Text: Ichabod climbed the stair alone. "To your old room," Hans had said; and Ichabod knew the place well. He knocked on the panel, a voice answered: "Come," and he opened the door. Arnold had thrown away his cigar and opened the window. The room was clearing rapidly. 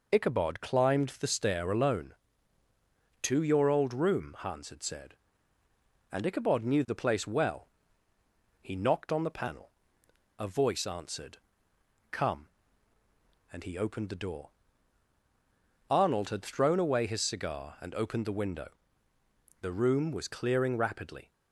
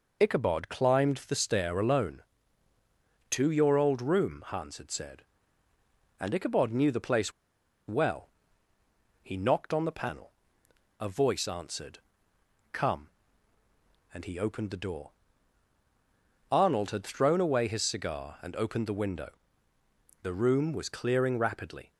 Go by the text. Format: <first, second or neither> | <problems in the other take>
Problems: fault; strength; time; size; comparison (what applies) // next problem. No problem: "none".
first | pauses between "place" and "well"; noticeable; at 7.3 s; 0.55 s long